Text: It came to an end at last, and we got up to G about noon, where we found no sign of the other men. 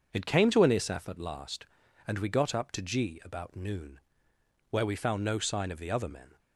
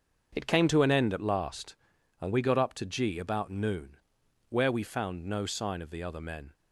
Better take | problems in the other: second | starts louder than the rest; until 1.1 s; 6.5 dB; also in the second // says "isaf" for "end"; at 0.7 s

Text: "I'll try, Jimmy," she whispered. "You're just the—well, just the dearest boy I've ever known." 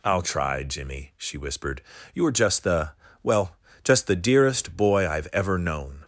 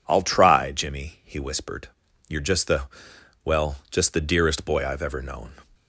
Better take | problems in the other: first | says "he" for "she"; at 1.2 s

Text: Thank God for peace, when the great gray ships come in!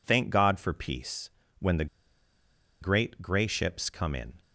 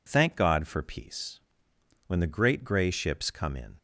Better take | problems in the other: second | pauses between "the" and "great"; noticeable; at 1.8 s; 0.95 s long

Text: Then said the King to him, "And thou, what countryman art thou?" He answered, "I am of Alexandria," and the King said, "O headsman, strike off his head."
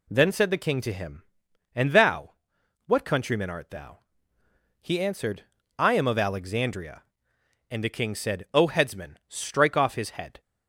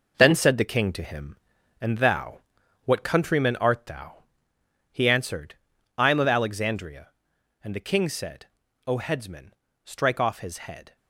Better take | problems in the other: first | gets quieter; strong; throughout; 8 dB

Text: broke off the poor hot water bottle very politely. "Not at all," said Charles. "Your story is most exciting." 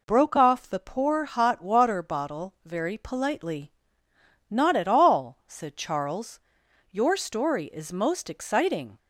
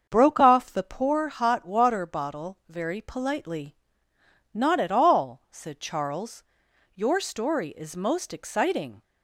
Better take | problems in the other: first | starts louder than the rest; until 1.2 s; 7 dB

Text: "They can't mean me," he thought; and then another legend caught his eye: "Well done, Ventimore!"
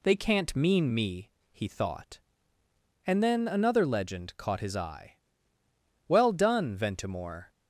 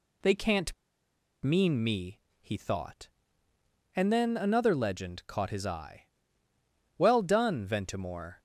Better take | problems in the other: first | pauses between "can't" and "mean"; noticeable; at 0.7 s; 0.70 s long

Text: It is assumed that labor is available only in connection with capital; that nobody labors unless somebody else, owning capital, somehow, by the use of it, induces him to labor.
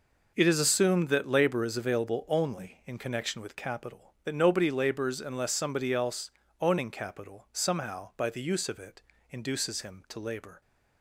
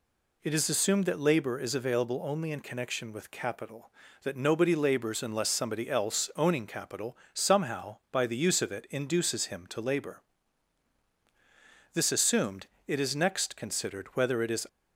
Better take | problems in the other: first | goes on to say "This assumed it is next considered whether it is"; strong; from 11.9 s on; 2.7 s long

